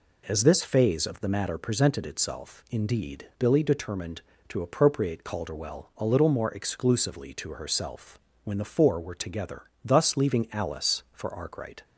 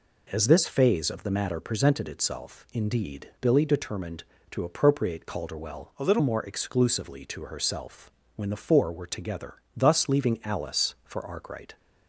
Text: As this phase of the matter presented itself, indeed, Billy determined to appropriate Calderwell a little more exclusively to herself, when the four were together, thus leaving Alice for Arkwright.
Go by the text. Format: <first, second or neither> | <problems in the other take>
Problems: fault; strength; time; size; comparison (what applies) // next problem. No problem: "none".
first | changes voice from "a" to "little"; from 5.9 to 6.1 s; 0.2 s long